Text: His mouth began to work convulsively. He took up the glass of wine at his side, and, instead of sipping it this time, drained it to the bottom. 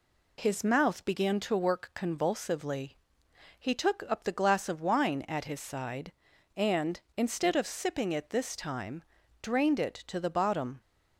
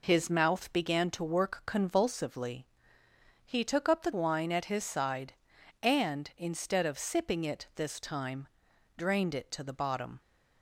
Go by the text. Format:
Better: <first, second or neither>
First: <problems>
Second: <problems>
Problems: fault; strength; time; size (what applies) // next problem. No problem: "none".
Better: first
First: none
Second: skips "glass of"; at 4.1 s